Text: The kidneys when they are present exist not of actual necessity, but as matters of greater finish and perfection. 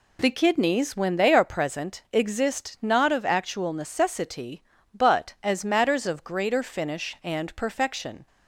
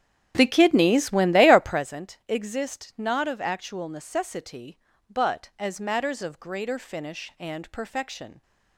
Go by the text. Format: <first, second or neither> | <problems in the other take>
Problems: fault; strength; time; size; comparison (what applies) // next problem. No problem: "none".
first | starts louder than the rest; strong; until 1.9 s; 9.5 dB